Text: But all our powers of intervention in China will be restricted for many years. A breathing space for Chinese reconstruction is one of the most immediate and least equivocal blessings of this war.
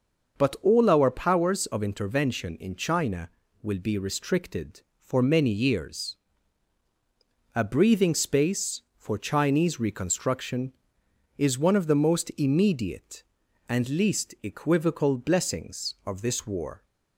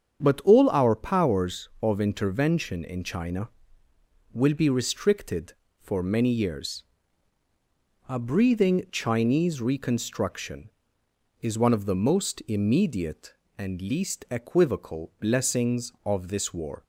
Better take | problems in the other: first | starts louder than the rest; strong; until 1.2 s; 8 dB; also in the first // skips "space for"; at 8.8 s

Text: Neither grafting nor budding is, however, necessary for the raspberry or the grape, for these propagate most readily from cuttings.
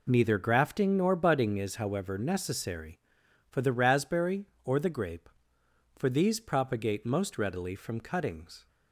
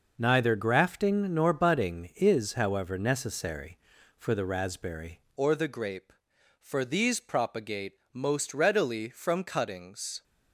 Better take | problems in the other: first | changes voice at "or"; from 5.3 s on; 4.9 s long // pauses between "propagate" and "most"; slight; at 7.9 s; 0.22 s long

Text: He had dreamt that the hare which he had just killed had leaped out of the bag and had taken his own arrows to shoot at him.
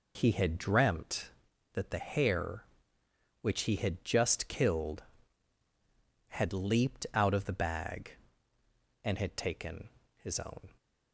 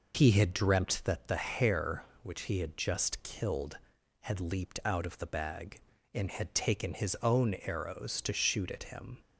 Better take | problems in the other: second | pauses between "taken" and "his"; slight; at 9.9 s; 0.26 s long // stops before "arrows to shoot at him"; at 10.7 s

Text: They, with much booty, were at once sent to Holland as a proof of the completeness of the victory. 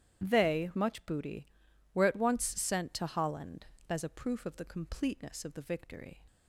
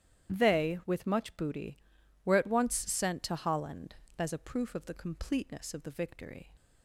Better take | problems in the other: second | starts louder than the rest; strong; until 1.2 s; 11 dB; strong in the second // skips "with"; at 0.7 s

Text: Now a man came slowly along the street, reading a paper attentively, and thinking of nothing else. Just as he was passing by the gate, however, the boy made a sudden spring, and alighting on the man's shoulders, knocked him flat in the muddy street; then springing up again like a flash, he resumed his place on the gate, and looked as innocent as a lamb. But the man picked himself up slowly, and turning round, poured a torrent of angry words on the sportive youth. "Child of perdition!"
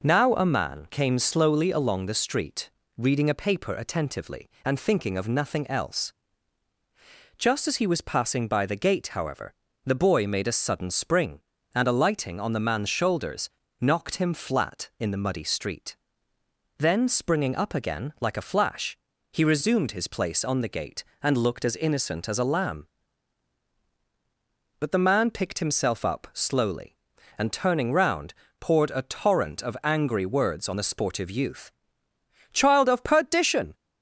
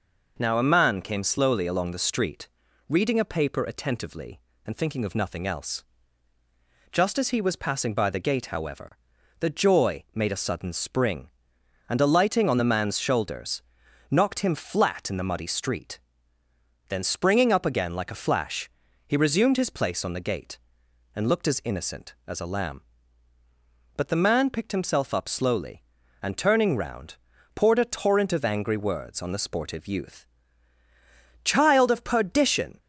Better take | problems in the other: first | says "joy" for "boy"; at 9.4 s

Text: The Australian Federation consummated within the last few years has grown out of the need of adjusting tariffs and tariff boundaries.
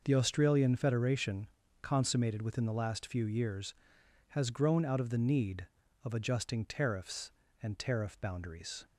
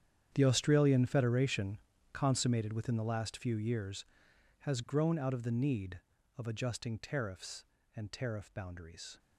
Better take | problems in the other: first | gets quieter; strong; throughout; 17 dB // pauses between "Federation" and "consummated"; slight; at 1.7 s; 0.36 s long; slight in the first

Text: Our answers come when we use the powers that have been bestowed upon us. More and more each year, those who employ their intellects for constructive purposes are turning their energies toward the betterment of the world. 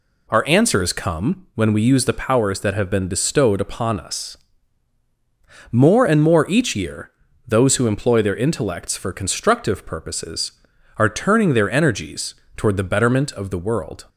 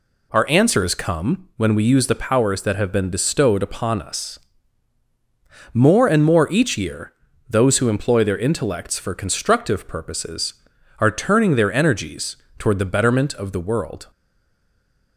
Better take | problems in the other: first | pauses between "energies" and "toward"; slight; at 12.3 s; 0.22 s long; slight in the first // stays silent after the last word; from 14.1 s on; 1.0 s long

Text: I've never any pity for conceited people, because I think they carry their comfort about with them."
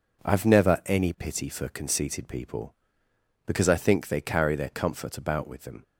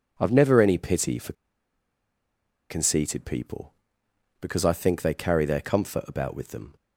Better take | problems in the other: first | pauses between "for" and "conceited"; strong; at 1.3 s; 1.3 s long

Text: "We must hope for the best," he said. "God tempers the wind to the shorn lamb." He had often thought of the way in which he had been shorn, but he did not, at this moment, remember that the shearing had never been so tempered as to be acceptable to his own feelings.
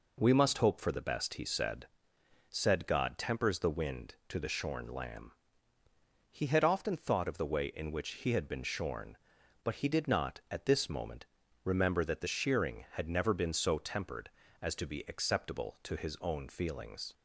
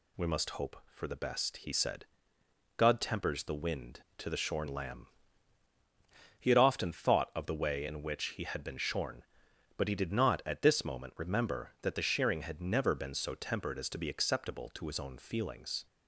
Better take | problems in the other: second | says "said" twice; at 2.4 s

